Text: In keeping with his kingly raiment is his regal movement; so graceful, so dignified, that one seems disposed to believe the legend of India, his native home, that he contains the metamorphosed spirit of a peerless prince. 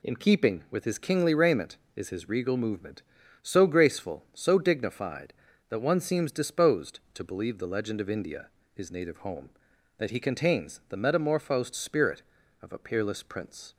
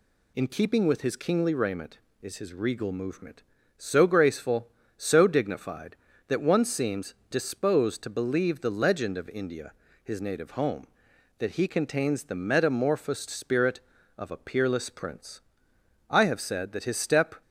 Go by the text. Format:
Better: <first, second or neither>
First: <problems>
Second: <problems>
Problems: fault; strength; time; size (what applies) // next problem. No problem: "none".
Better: first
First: none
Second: pauses between "seems" and "disposed"; slight; at 7.1 s; 0.16 s long // goes on to say "I have said that his step"; noticeable; from 16.1 s on; 1.3 s long